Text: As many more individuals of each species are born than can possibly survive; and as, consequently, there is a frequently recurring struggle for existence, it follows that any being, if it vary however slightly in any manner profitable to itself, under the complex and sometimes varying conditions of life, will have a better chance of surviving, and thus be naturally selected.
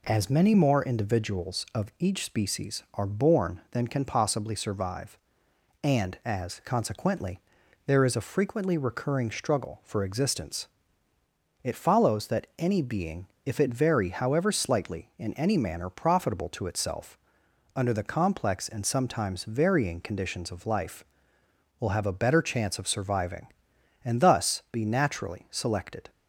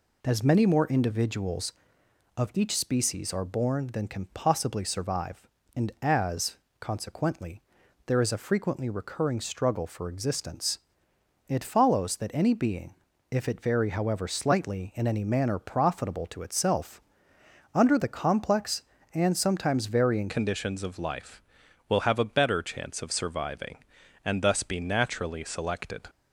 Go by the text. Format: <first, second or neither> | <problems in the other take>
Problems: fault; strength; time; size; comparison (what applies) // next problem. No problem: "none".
first | changes voice at "conditions"; from 20.2 s on; 5.8 s long